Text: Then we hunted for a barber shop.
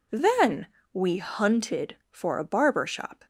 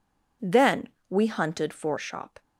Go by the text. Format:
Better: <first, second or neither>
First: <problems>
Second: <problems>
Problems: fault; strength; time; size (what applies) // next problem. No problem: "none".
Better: first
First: pauses between "Then" and "we"; slight; at 0.6 s; 0.24 s long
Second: pauses between "Then" and "we"; slight; at 0.8 s; 0.22 s long // skips "a barber"; at 1.9 s